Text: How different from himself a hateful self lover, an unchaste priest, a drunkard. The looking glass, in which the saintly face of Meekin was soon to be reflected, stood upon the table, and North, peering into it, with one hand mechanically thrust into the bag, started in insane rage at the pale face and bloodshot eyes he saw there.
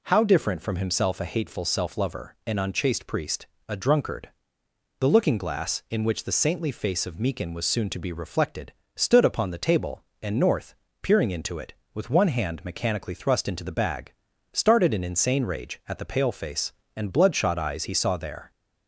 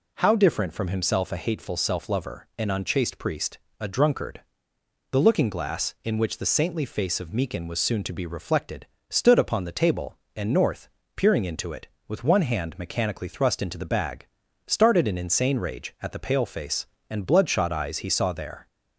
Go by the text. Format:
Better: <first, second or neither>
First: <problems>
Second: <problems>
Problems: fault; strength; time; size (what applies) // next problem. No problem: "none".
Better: neither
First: none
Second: none